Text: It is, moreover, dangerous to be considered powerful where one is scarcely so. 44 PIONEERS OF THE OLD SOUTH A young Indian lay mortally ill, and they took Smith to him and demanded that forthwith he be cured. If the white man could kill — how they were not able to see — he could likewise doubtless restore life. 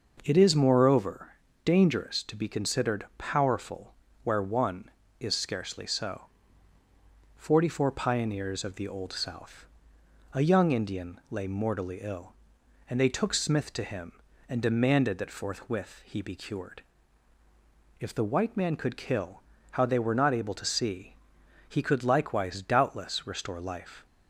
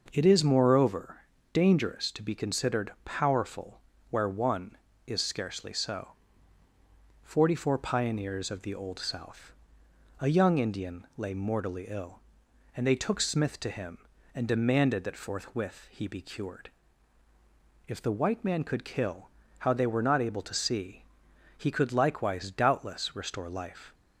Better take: neither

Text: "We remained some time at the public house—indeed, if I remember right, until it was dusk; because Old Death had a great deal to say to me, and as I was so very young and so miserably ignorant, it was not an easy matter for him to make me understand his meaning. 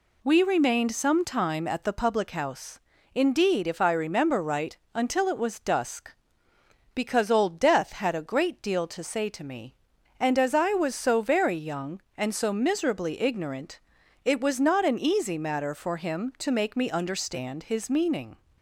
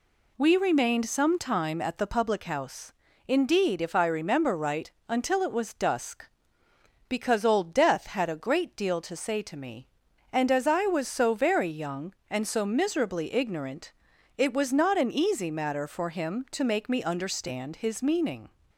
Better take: neither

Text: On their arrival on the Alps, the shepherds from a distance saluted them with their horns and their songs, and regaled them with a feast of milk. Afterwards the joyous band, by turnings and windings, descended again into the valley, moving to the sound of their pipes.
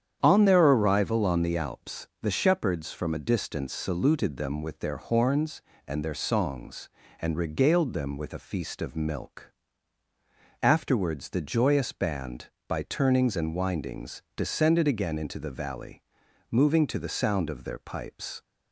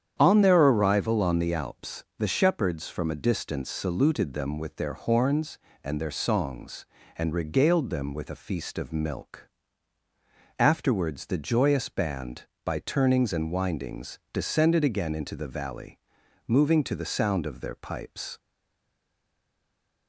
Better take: first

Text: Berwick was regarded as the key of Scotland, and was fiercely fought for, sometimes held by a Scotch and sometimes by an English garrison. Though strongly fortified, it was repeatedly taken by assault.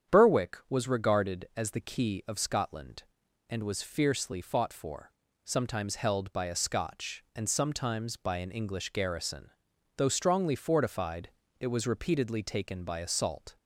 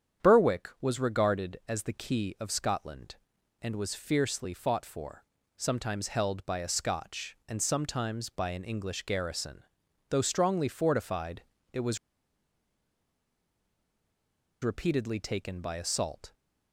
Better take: first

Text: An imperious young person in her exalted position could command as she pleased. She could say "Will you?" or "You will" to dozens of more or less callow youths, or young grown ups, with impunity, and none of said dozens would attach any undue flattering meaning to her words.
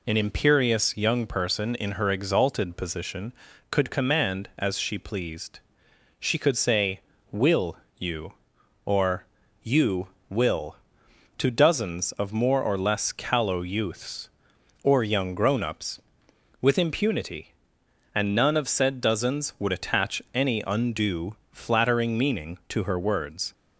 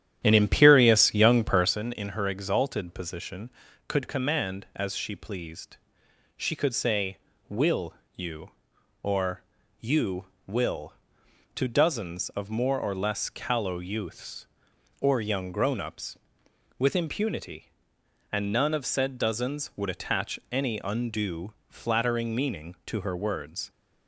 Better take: first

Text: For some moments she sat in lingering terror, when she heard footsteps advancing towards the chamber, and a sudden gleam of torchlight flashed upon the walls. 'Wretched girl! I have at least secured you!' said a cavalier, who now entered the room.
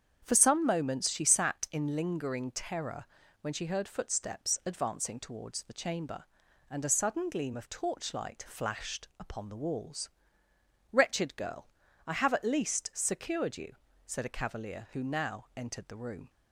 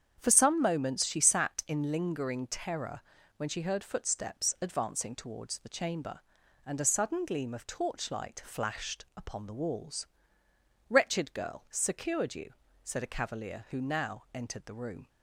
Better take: first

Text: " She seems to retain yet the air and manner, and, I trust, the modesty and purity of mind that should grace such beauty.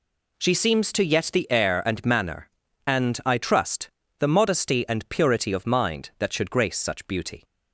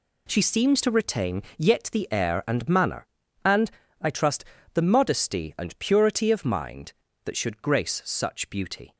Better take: second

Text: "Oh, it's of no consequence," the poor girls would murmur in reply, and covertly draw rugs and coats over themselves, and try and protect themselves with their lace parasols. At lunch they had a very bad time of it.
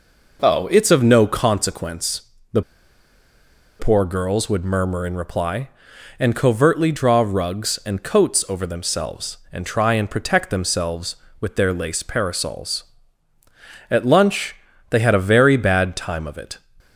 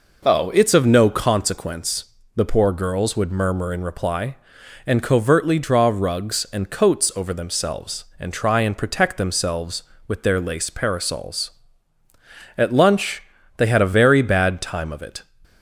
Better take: second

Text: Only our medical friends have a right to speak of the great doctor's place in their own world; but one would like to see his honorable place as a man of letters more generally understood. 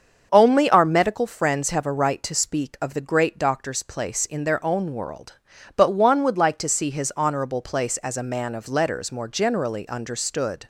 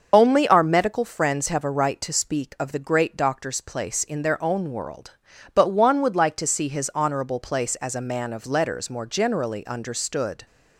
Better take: first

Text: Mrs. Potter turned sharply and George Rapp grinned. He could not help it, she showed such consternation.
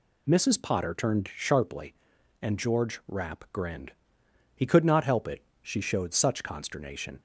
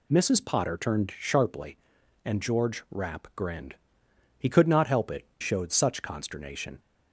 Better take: first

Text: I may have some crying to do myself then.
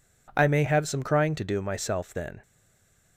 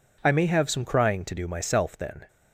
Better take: second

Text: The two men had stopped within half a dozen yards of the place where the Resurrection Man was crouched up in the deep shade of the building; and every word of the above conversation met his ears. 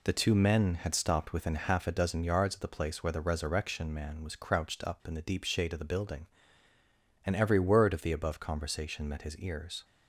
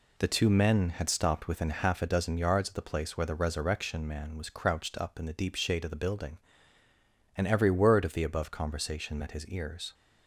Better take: neither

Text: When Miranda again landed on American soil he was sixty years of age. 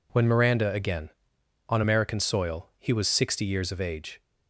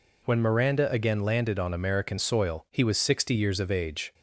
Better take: second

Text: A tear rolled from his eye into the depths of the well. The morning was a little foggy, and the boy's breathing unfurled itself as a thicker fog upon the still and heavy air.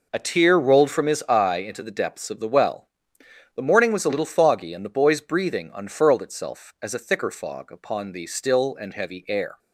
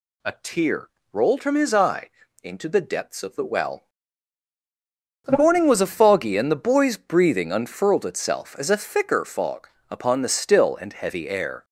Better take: first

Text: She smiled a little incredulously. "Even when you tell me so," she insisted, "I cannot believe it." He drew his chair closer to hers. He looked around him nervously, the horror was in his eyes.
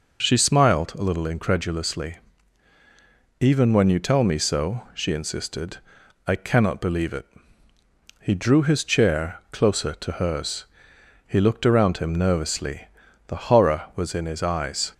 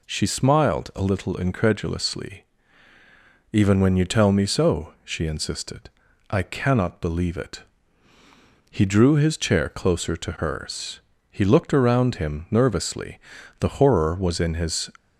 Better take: first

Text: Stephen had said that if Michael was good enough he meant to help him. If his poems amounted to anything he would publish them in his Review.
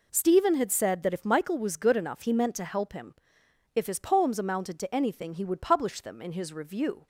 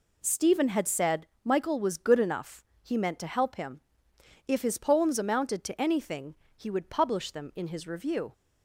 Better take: first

